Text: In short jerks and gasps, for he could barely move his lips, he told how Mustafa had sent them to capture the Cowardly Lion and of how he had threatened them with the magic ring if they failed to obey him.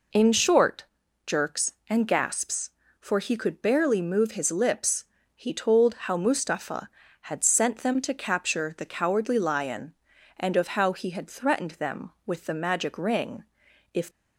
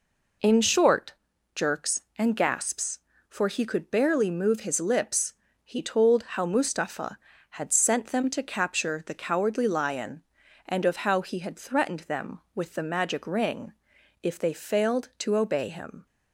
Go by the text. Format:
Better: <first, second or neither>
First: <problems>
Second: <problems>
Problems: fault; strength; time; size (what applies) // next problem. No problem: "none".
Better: second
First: pauses between "short" and "jerks"; at 0.8 s; 0.42 s long // pauses between "ring" and "if"; noticeable; at 13.4 s; 0.48 s long // stops before "they failed to obey him"; at 14.1 s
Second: pauses between "short" and "jerks"; at 1.1 s; 0.42 s long // pauses between "ring" and "if"; noticeable; at 13.7 s; 0.48 s long